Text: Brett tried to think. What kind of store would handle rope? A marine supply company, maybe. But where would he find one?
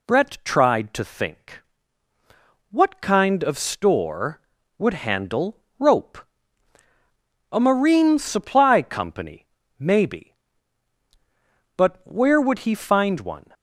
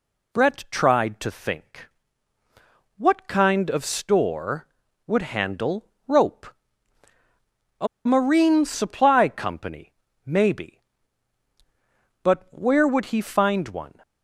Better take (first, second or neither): first